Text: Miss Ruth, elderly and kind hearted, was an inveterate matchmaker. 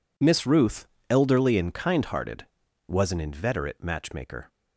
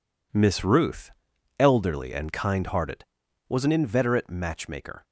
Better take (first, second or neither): neither